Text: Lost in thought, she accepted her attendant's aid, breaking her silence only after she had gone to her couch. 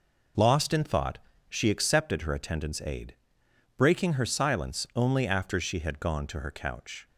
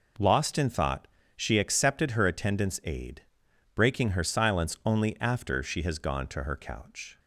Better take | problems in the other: first | says "has" for "had"; at 5.8 s

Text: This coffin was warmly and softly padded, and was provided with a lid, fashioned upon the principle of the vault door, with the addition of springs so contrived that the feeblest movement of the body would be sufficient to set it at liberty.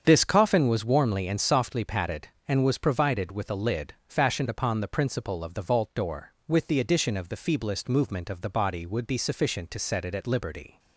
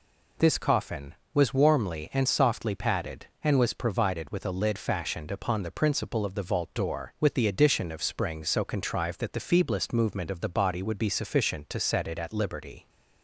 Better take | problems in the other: second | starts louder than the rest; strong; until 1.0 s; 7.5 dB // skips "springs so contrived that"; at 7.2 s

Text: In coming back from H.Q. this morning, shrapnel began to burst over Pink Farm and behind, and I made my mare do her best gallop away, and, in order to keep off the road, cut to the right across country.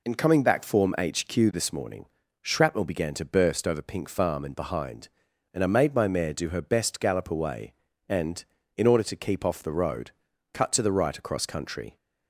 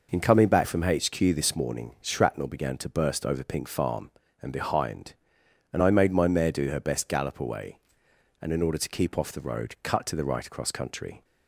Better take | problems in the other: second | says "form" for "from"; at 0.6 s

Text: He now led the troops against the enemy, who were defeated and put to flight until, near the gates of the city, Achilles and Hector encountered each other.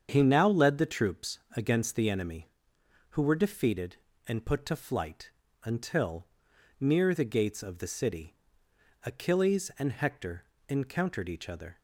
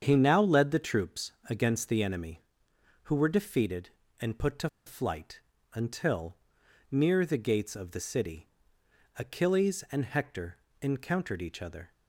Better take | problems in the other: first | starts louder than the rest; strong; until 1.0 s; 7.5 dB; strong in the first // pauses between "troops" and "against"; slight; at 1.3 s; 0.18 s long; slight in the first // pauses between "to" and "flight"; slight; at 4.6 s; 0.19 s long // pauses between "flight" and "until"; slight; at 5.3 s; 0.34 s long; slight in the first // pauses between "Hector" and "encountered"; slight; at 10.5 s; 0.24 s long; slight in the first

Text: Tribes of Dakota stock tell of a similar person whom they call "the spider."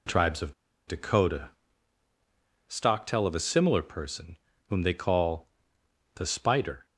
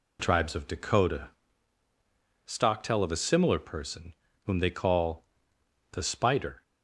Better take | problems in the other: second | pauses between "of" and "Dakota"; slight; at 0.5 s; 0.33 s long // pauses between "Dakota" and "stock"; at 1.4 s; 1.1 s long; also in the second // pauses between "person" and "whom"; slight; at 4.3 s; 0.34 s long; slight in the second // pauses between "call" and "the"; noticeable; at 5.4 s; 0.68 s long; noticeable in the second

